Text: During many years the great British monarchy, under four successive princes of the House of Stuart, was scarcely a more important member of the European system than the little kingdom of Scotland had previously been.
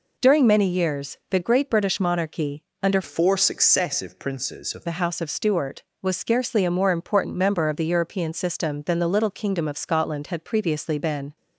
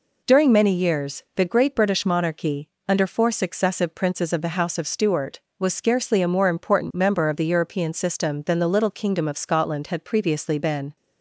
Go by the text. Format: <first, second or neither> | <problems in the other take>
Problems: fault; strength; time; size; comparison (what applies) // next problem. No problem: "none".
second | changes voice from "four" to "of"; from 3.0 to 4.8 s; 1.8 s long